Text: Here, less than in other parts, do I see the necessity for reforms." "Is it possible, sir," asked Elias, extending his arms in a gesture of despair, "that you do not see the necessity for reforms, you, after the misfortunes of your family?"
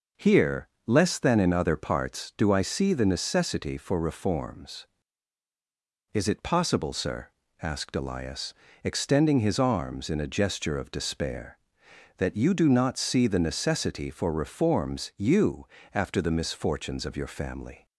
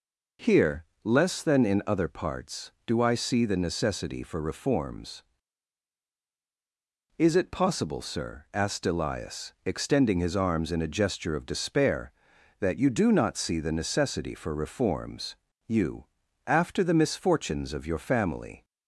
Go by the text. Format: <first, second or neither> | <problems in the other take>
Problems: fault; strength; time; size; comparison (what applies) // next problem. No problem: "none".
neither | none